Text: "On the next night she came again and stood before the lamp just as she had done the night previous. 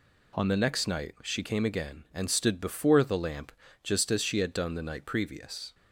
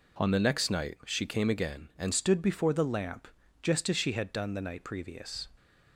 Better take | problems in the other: first | changes voice at "stood"; from 2.1 s on; 3.3 s long // pauses between "lamp" and "just"; slight; at 3.2 s; 0.34 s long; slight in the first

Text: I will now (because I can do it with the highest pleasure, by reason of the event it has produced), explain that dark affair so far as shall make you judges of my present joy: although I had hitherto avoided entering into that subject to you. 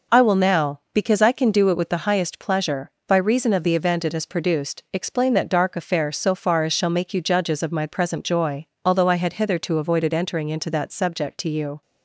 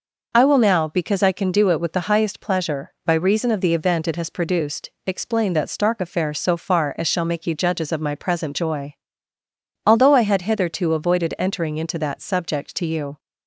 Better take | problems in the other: first | says "stark" for "dark"; at 5.7 s

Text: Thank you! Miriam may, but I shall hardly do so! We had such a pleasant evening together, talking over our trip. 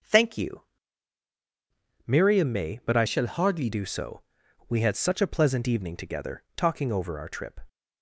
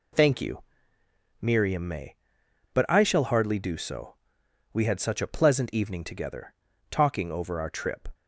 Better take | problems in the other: second | starts louder than the rest; until 2.4 s; 6 dB // changes voice from "shall" to "hardly"; from 3.0 to 3.6 s; 0.6 s long

